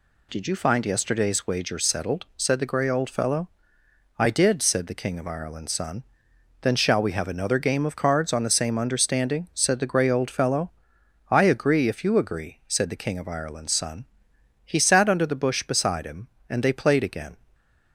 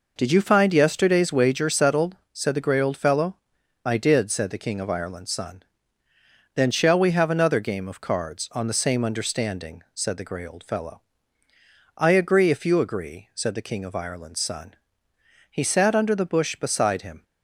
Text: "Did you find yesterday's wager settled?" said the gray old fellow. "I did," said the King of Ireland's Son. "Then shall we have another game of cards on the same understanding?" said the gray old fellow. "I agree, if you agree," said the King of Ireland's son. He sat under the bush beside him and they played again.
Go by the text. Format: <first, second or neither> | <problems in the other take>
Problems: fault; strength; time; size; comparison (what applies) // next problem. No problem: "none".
first | stops before "and they played again"; at 17.2 s